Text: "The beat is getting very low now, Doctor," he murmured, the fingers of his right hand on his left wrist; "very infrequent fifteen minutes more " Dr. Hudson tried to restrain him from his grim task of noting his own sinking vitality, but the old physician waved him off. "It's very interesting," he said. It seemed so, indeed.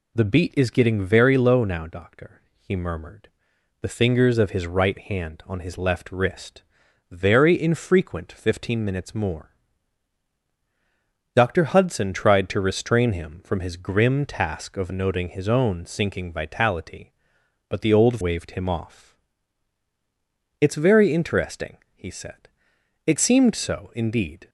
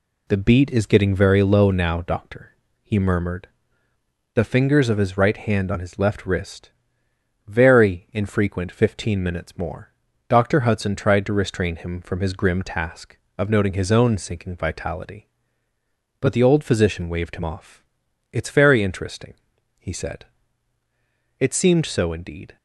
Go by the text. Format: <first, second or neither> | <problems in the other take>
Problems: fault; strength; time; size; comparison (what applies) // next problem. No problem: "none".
second | skips "physician"; at 18.1 s